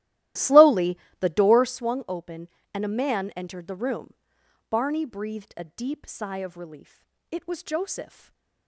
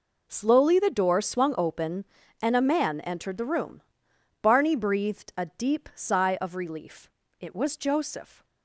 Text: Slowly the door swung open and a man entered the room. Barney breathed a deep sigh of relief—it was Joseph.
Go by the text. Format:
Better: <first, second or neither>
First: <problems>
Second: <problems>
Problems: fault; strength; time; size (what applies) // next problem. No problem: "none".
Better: second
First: starts louder than the rest; strong; until 1.8 s; 15 dB // pauses between "Slowly" and "the"; slight; at 0.9 s; 0.22 s long // stays silent after the last word; slight; from 8.0 s on; 0.6 s long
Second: none